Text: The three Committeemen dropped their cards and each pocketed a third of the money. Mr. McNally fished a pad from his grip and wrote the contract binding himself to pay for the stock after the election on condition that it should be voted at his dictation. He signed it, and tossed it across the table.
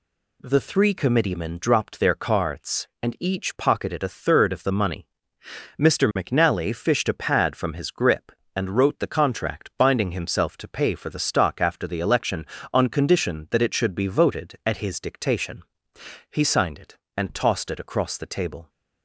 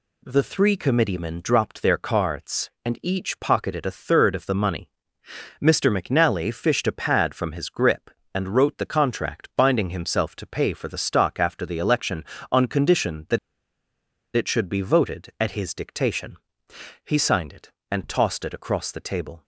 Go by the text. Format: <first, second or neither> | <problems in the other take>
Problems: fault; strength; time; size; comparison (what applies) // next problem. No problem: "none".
first | pauses between "that" and "it"; at 13.3 s; 0.98 s long